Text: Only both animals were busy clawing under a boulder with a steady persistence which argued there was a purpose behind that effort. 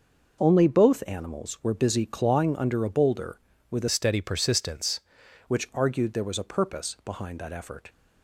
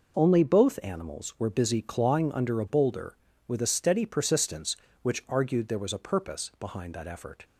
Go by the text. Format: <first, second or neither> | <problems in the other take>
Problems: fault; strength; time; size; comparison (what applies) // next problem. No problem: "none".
second | changes voice from "steady" to "persistence"; from 3.8 to 4.9 s; 1.1 s long